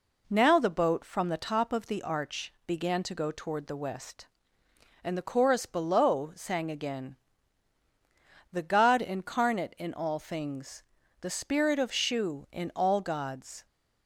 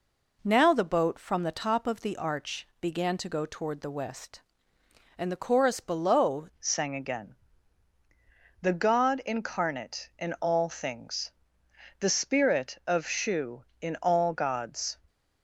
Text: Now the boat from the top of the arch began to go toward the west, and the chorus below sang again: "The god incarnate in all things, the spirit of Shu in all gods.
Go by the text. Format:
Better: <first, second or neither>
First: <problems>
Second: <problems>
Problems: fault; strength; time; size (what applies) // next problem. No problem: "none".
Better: first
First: none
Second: changes voice at "sang"; from 6.6 s on; 8.3 s long